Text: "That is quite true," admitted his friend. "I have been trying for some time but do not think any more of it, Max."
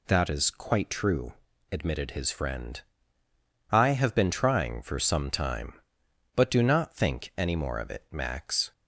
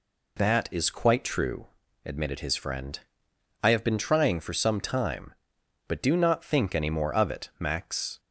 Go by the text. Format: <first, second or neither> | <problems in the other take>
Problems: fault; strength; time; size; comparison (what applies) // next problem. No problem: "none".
neither | none